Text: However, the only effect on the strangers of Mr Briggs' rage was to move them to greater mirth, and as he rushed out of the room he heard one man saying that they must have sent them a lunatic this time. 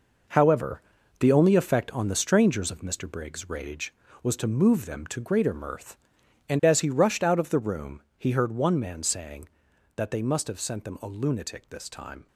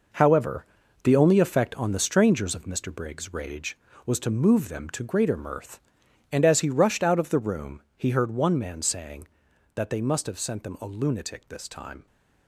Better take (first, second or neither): neither